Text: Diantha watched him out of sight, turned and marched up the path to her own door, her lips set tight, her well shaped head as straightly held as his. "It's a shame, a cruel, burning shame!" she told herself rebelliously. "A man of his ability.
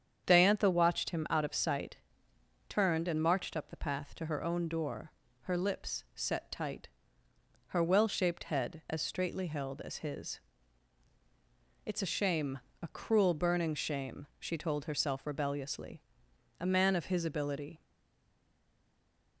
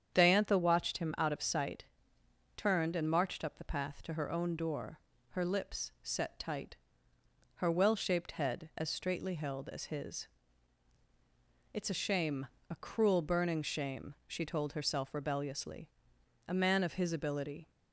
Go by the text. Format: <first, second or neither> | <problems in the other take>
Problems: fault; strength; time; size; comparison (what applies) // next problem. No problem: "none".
second | starts louder than the rest; strong; until 1.2 s; 8 dB; strong in the second // stays silent after the last word; noticeable; from 17.8 s on; 1.6 s long